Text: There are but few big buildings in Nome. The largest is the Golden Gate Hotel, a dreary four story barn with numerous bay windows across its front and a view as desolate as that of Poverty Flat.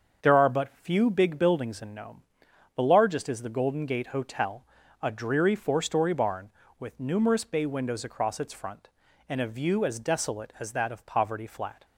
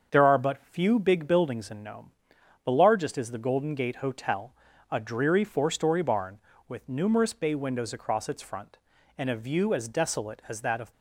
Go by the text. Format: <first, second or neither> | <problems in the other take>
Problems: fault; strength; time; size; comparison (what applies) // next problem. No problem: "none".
first | starts louder than the rest; until 1.1 s; 7 dB; also in the first // stops before "Poverty Flat"; at 10.9 s